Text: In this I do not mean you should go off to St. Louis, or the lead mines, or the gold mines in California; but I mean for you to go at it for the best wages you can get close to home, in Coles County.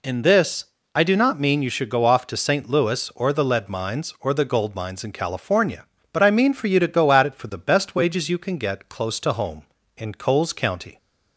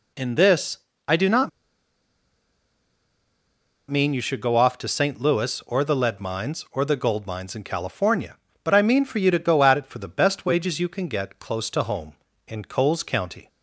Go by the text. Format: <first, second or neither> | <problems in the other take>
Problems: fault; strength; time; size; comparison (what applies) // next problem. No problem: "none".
first | pauses between "this" and "I"; slight; at 0.7 s; 0.30 s long; slight in the first // pauses between "not" and "mean"; strong; at 1.4 s; 2.4 s long